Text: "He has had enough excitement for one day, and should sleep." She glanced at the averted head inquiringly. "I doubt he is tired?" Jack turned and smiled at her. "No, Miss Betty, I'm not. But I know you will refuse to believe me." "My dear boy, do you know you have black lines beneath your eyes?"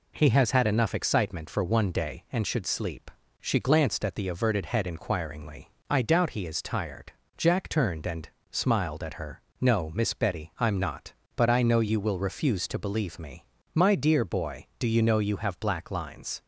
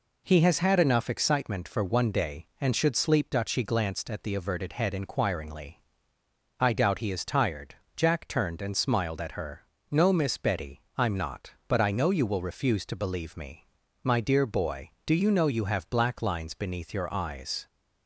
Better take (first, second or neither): second